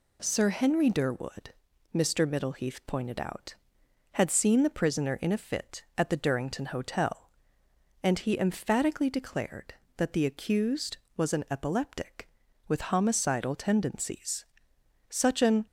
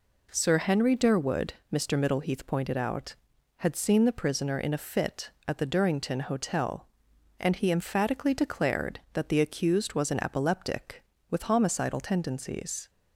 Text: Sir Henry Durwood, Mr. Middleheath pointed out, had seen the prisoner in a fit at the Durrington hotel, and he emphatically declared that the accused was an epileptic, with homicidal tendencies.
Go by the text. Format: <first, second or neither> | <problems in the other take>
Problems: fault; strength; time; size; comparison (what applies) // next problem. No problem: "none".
second | goes on to say "Such an"; from 15.0 s on; 0.56 s long